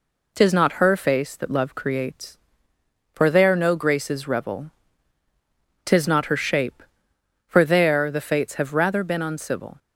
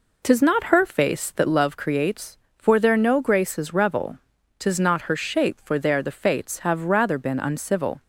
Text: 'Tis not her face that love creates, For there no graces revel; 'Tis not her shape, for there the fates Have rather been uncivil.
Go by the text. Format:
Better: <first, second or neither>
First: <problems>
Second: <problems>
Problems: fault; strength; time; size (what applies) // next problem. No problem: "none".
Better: neither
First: none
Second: none